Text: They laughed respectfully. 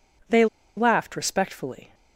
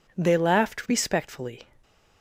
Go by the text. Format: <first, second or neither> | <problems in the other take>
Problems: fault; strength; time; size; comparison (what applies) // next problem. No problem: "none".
second | pauses between "They" and "laughed"; slight; at 0.4 s; 0.31 s long